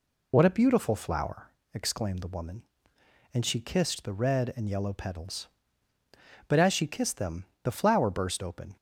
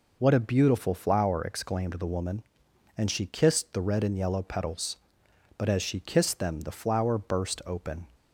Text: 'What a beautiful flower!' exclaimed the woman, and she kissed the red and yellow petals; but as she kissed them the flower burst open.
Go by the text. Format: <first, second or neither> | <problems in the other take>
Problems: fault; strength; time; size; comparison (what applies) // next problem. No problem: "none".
second | loses the start of "What"; at 0.3 s; 35 ms // pauses between "them" and "the"; slight; at 7.4 s; 0.18 s long